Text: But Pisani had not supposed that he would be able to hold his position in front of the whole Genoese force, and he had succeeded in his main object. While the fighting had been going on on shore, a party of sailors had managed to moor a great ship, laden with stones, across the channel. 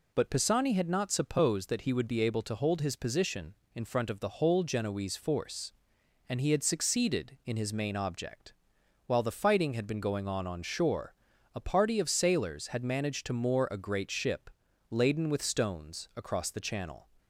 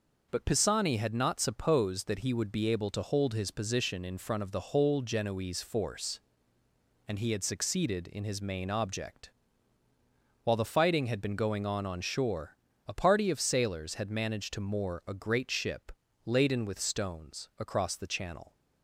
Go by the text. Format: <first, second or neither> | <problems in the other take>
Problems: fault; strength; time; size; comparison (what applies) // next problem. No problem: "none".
neither | none